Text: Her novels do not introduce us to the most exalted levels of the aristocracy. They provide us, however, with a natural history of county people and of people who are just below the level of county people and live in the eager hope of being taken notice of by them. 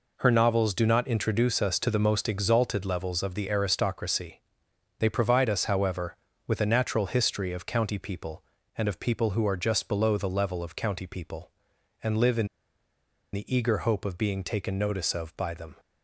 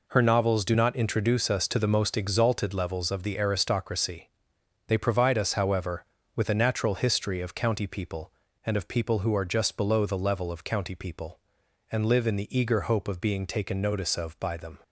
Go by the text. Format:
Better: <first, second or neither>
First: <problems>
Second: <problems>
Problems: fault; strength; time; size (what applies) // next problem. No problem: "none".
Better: second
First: pauses between "in" and "the"; noticeable; at 12.4 s; 0.85 s long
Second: none